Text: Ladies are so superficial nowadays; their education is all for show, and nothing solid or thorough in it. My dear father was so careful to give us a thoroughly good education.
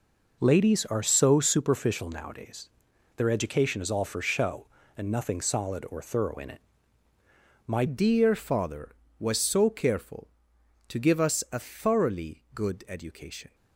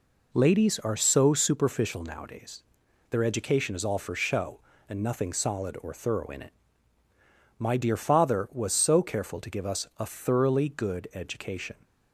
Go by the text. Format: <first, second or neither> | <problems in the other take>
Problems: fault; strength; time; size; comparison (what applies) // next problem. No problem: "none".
second | changes voice at "dear"; from 7.8 s on; 5.7 s long